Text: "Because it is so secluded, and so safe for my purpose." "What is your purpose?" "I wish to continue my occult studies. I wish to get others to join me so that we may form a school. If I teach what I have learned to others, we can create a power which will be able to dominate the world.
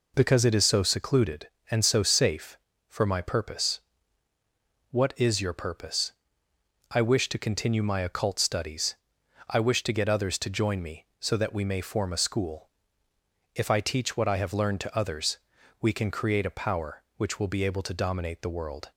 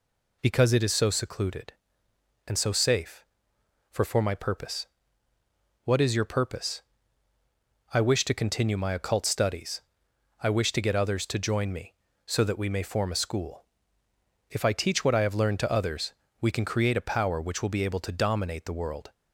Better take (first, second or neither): first